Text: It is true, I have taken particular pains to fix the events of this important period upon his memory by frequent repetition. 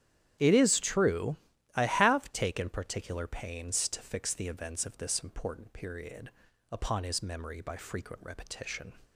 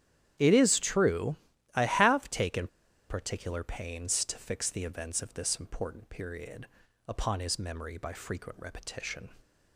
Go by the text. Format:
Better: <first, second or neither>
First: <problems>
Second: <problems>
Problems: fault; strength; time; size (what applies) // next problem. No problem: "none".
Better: first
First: starts louder than the rest; strong; until 1.8 s; 10.5 dB // pauses between "period" and "upon"; at 6.2 s; 0.42 s long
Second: starts louder than the rest; strong; until 1.7 s; 10.5 dB // pauses between "taken" and "particular"; at 2.6 s; 0.43 s long // pauses between "period" and "upon"; at 6.6 s; 0.42 s long